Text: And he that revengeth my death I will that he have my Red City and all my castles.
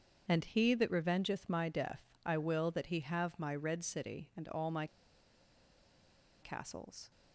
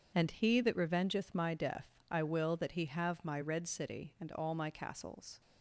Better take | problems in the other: second | starts louder than the rest; strong; until 1.2 s; 7 dB // pauses between "death" and "I"; slight; at 2.0 s; 0.22 s long; slight in the second // pauses between "my" and "castles"; strong; at 4.8 s; 1.5 s long

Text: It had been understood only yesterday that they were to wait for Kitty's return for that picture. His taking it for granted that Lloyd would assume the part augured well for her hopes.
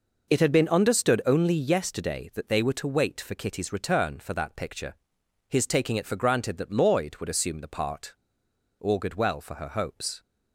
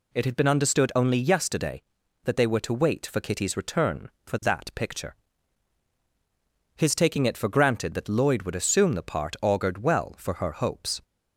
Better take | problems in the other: second | pauses between "part" and "augured"; noticeable; at 8.1 s; 0.67 s long

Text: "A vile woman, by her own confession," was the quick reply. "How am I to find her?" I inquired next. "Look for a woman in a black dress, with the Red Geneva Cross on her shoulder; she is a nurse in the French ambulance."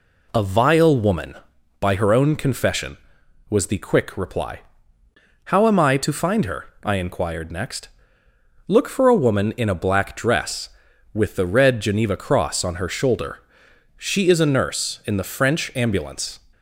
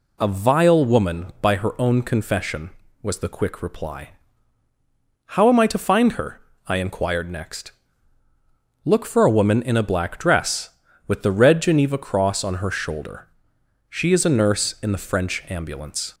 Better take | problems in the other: neither | none

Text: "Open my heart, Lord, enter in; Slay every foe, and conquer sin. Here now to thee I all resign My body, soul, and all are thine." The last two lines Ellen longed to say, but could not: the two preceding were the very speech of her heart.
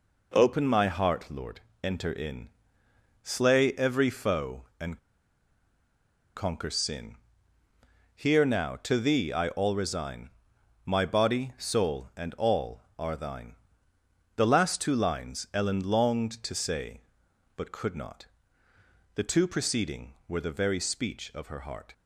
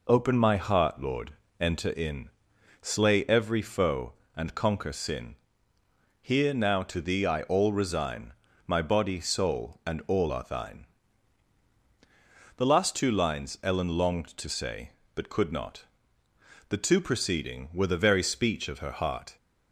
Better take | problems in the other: second | pauses between "and" and "conquer"; strong; at 4.9 s; 1.3 s long // pauses between "resign" and "My"; noticeable; at 10.3 s; 0.56 s long; slight in the second

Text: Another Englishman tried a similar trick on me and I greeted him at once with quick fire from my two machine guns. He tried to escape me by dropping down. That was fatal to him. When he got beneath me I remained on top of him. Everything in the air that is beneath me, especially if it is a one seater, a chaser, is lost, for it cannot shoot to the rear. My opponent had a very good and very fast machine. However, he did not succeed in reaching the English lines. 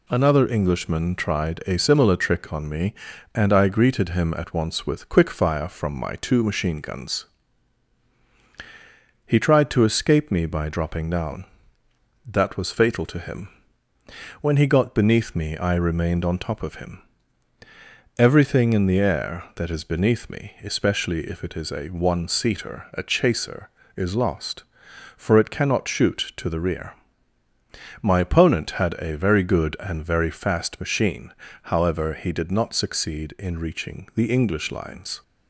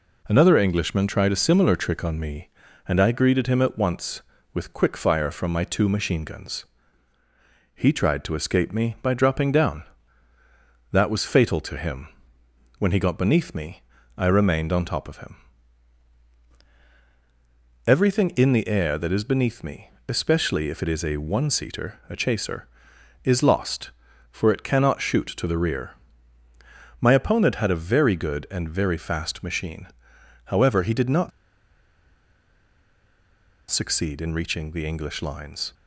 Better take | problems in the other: first | pauses between "me" and "I"; slight; at 13.8 s; 0.34 s long // pauses between "not" and "succeed"; strong; at 31.3 s; 2.4 s long

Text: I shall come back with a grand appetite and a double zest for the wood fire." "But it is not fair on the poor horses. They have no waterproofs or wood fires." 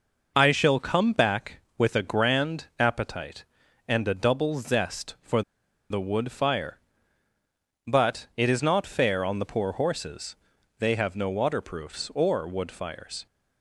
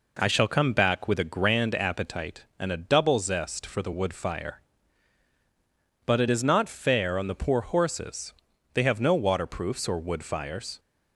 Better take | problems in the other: second | pauses between "for" and "the"; noticeable; at 5.4 s; 0.49 s long

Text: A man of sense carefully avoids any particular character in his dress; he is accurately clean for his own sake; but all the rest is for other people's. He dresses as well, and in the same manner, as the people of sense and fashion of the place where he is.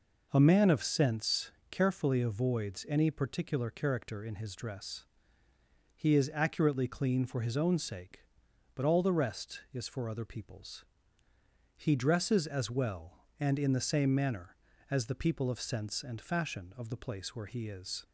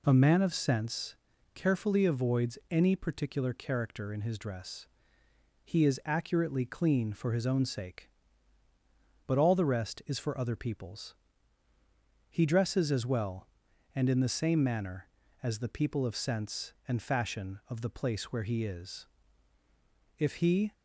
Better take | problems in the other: first | pauses between "sense" and "carefully"; at 1.1 s; 0.40 s long; slight in the first // goes on to say "If he"; from 20.1 s on; 0.54 s long

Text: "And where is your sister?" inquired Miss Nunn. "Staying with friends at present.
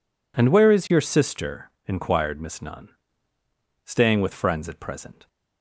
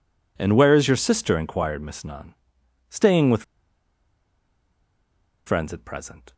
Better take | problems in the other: first | pauses between "with" and "friends"; strong; at 3.4 s; 2.0 s long

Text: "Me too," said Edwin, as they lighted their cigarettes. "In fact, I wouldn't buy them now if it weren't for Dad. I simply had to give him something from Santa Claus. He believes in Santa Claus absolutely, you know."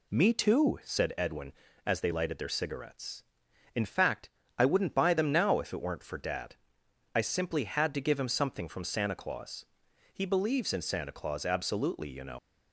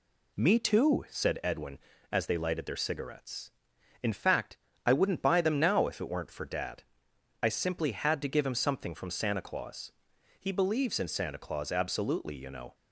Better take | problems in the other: second | leaves "know" unfinished; at 12.3 s; 95 ms

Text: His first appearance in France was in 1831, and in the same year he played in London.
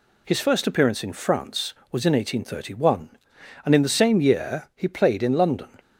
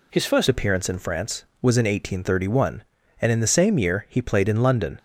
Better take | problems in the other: first | changes voice at "appearance"; from 0.4 s on; 4.5 s long

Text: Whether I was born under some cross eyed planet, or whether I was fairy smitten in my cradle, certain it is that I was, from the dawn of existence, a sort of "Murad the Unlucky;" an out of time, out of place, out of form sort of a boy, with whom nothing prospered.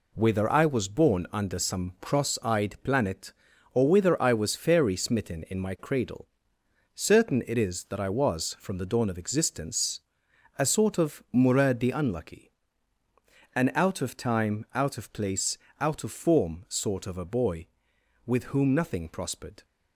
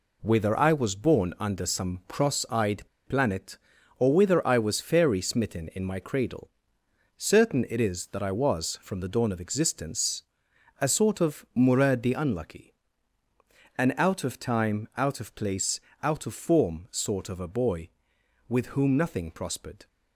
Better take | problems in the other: first | pauses between "eyed" and "planet"; slight; at 2.8 s; 0.25 s long

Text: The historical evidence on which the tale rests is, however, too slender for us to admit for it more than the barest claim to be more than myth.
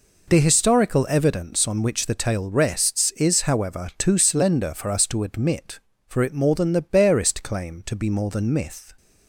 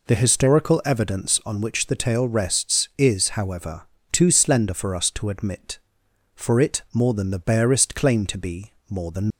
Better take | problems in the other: first | pauses between "be" and "more"; slight; at 8.7 s; 0.18 s long // stops before "myth"; at 9.3 s

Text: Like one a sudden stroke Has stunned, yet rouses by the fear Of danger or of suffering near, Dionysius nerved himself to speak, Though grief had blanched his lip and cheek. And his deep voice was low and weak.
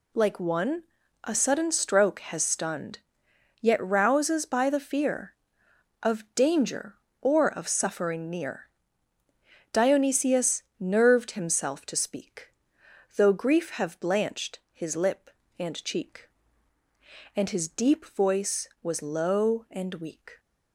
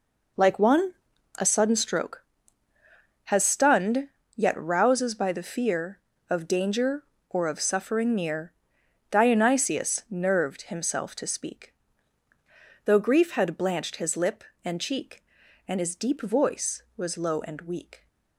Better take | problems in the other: second | pauses between "one" and "a"; at 0.8 s; 0.40 s long; also in the second // pauses between "Dionysius" and "nerved"; slight; at 10.6 s; 0.16 s long // says "have" for "had"; at 13.7 s

